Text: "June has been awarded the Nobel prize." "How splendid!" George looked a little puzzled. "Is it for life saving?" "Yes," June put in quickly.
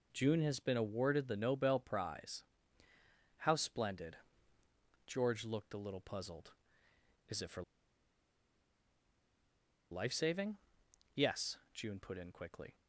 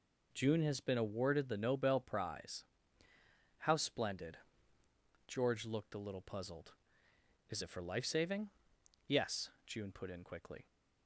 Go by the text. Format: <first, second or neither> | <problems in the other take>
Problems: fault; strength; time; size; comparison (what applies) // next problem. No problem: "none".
second | pauses between "for" and "life"; strong; at 7.6 s; 2.2 s long